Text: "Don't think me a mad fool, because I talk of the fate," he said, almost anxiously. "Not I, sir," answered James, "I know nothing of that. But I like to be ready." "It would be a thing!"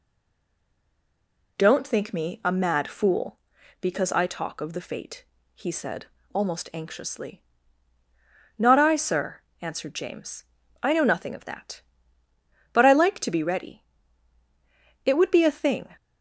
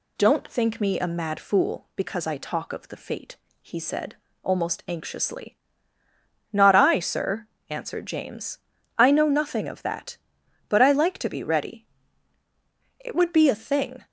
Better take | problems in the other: second | stays silent before the first word; noticeable; until 1.5 s; 1.5 s long

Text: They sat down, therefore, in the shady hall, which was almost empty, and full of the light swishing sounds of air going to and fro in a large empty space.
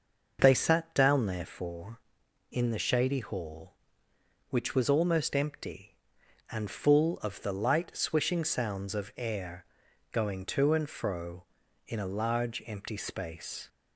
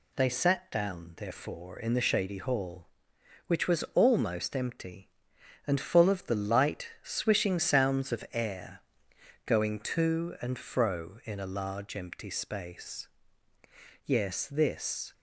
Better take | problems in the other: first | pauses between "air" and "going"; noticeable; at 8.8 s; 0.64 s long; noticeable in the first // goes on to say "Yes this"; noticeable; from 14.0 s on; 1.0 s long

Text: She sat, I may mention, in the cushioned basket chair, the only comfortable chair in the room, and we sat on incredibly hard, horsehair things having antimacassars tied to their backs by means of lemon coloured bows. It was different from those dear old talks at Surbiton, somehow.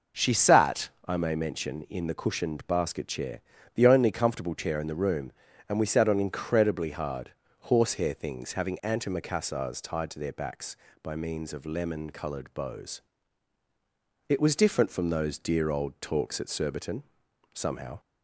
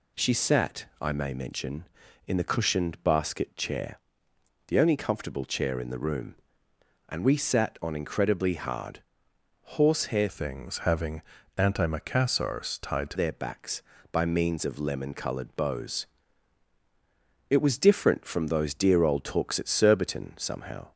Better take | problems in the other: first | changes voice from "things" to "to"; from 10.2 to 13.1 s; 2.9 s long // pauses between "having" and "antimacassars"; slight; at 11.2 s; 0.36 s long

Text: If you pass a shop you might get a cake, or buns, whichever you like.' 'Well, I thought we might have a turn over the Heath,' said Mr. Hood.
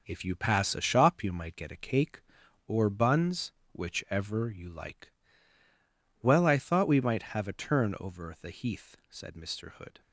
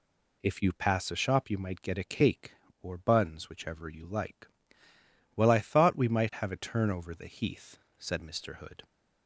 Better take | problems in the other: second | gets quieter; noticeable; throughout; 6 dB

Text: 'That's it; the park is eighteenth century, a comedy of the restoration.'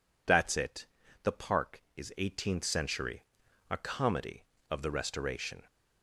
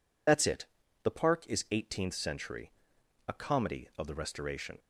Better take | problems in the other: first | loses the start of "That's"; at 0.2 s; 50 ms

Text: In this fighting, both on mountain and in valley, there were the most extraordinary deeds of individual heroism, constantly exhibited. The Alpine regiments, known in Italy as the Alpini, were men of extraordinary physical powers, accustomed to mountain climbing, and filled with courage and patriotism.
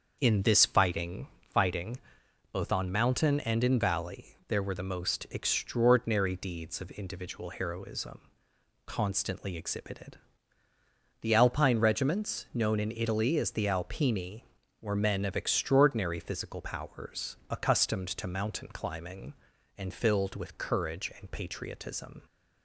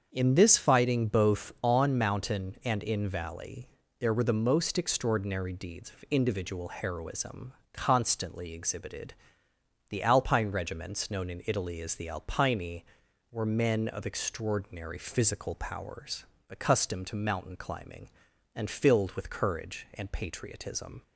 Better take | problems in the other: second | starts louder than the rest; until 1.2 s; 6.5 dB; also in the second // says "fighting" twice; at 1.5 s

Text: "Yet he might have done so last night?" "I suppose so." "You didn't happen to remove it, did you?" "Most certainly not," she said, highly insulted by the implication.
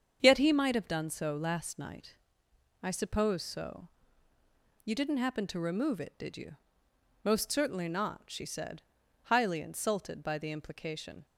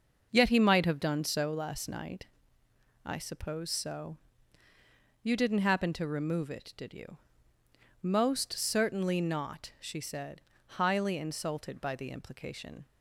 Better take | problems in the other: neither | starts louder than the rest; the same in both

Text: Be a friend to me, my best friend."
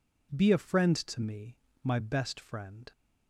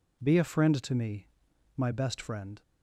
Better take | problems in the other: neither | none

